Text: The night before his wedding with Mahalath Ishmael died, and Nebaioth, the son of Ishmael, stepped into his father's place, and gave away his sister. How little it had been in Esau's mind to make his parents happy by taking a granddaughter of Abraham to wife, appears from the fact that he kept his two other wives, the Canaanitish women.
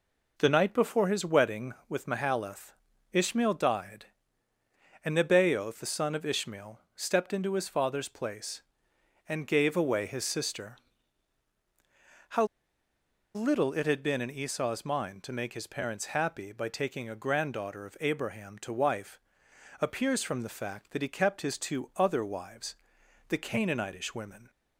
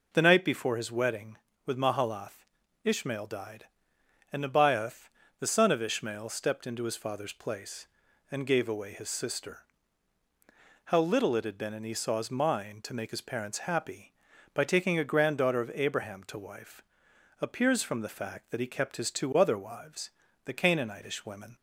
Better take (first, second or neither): second